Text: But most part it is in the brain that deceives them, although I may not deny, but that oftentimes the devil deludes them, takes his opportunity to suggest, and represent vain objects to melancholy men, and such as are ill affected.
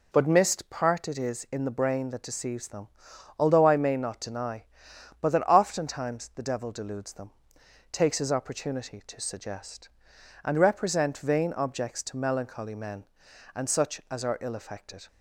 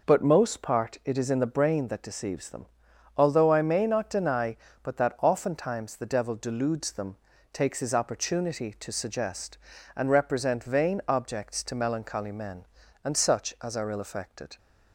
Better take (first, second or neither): second